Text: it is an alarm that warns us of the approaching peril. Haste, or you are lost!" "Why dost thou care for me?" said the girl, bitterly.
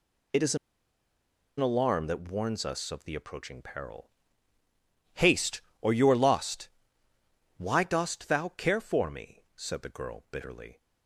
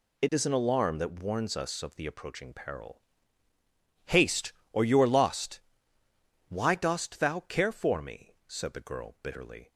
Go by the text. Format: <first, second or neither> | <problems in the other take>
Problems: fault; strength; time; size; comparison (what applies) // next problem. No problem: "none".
second | pauses between "an" and "alarm"; at 0.5 s; 1.0 s long